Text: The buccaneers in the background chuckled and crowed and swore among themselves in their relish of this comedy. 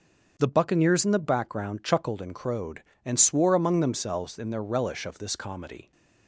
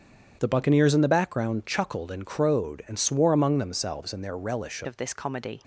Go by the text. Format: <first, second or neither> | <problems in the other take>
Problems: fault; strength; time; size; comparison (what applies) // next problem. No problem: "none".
first | starts louder than the rest; strong; until 1.4 s; 8.5 dB; also in the first // changes voice at "of"; from 4.8 s on; 0.8 s long